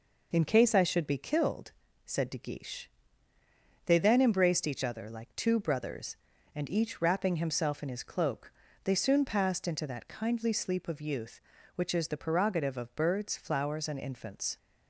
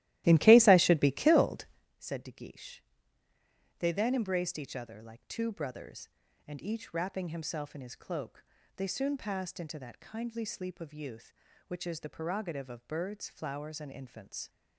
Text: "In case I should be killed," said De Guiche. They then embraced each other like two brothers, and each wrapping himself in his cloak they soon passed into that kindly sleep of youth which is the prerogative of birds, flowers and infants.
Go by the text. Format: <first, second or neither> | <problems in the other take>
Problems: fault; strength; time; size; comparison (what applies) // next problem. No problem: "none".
first | starts louder than the rest; strong; until 1.9 s; 15.5 dB // pauses between "cloak" and "they"; slight; at 8.4 s; 0.32 s long; slight in the first